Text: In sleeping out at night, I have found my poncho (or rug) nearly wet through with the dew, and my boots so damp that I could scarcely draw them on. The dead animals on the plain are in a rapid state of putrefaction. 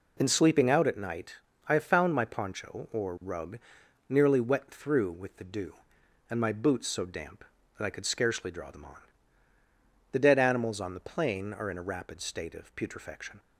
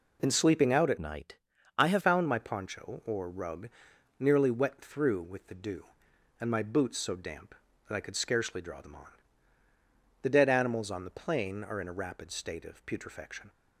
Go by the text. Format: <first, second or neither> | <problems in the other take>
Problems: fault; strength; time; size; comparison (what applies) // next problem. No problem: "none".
first | changes voice from "night" to "have"; from 0.9 to 2.0 s; 1.1 s long